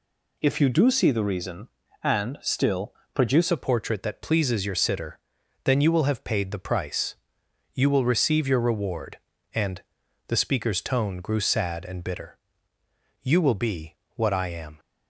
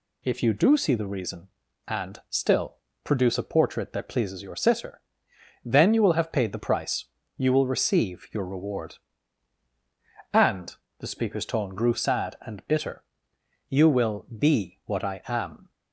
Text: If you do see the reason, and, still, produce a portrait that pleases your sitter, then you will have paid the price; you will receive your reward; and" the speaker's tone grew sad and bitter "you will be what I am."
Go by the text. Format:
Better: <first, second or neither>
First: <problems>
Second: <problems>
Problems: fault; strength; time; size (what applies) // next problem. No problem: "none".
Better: second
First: changes voice at "a"; from 3.5 s on; 11.2 s long // pauses between "and" and "the"; at 9.8 s; 0.42 s long // pauses between "bitter" and "you"; noticeable; at 12.3 s; 0.82 s long // pauses between "be" and "what"; slight; at 13.9 s; 0.22 s long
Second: pauses between "and" and "the"; slight; at 10.7 s; 0.24 s long // pauses between "bitter" and "you"; noticeable; at 13.0 s; 0.68 s long